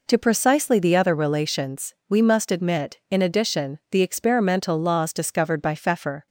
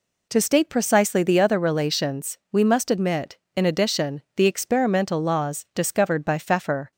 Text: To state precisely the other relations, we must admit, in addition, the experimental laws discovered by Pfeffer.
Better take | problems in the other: second | skips "state"; at 0.1 s

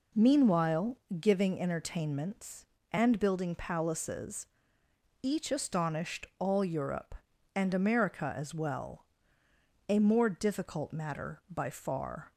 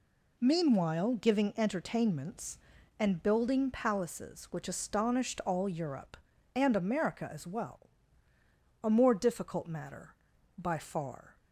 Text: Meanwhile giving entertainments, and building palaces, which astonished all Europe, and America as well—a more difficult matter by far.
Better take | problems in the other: second | pauses between "Meanwhile" and "giving"; slight; at 0.9 s; 0.20 s long // says "each" for "which"; at 5.2 s

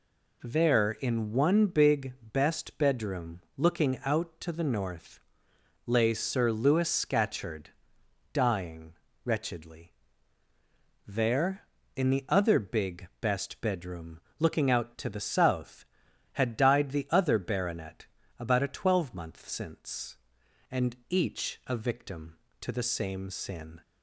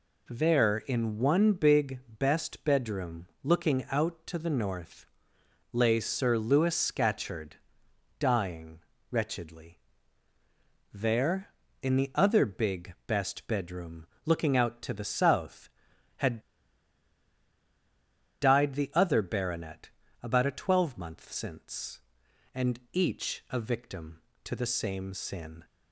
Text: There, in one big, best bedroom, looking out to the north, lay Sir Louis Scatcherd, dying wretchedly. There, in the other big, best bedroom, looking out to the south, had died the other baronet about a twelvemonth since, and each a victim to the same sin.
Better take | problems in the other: first | pauses between "dying" and "wretchedly"; slight; at 8.7 s; 0.32 s long; slight in the first // pauses between "had" and "died"; strong; at 16.3 s; 2.0 s long // pauses between "baronet" and "about"; slight; at 19.8 s; 0.34 s long; slight in the first

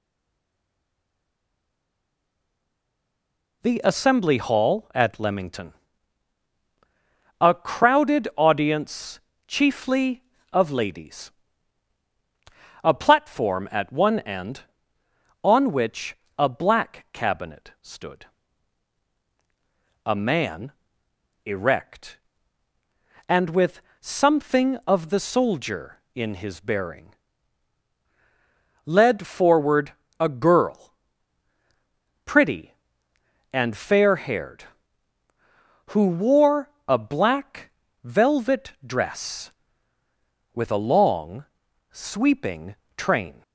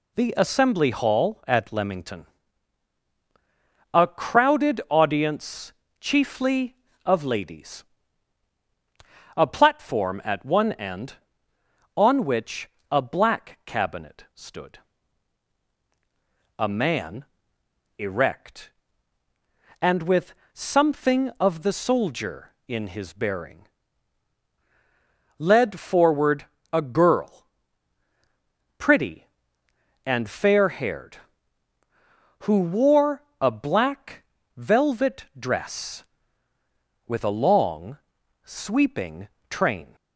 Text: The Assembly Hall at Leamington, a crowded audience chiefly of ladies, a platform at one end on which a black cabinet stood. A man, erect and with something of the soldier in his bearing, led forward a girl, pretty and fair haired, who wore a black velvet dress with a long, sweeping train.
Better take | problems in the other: second | stays silent before the first word; strong; until 3.6 s; 3.6 s long // pauses between "audience" and "chiefly"; slight; at 9.2 s; 0.26 s long; slight in the second // pauses between "which" and "a"; slight; at 16.1 s; 0.22 s long; slight in the second // pauses between "with" and "something"; slight; at 23.8 s; 0.18 s long; slight in the second // pauses between "forward" and "a"; slight; at 29.9 s; 0.26 s long; slight in the second // pauses between "wore" and "a"; slight; at 36.7 s; 0.16 s long; slight in the second // pauses between "black" and "velvet"; slight; at 37.7 s; 0.34 s long; slight in the second // pauses between "sweeping" and "train"; slight; at 42.7 s; 0.20 s long; slight in the second

